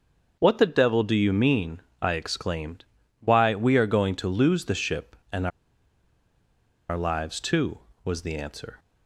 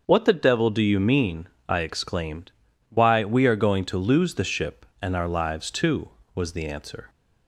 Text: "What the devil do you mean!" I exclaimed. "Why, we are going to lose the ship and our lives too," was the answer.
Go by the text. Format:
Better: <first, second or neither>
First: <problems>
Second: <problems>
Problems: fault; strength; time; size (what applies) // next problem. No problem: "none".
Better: second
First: starts louder than the rest; until 1.4 s; 6.5 dB // pauses between "and" and "our"; strong; at 5.4 s; 1.4 s long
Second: starts louder than the rest; until 1.0 s; 6.5 dB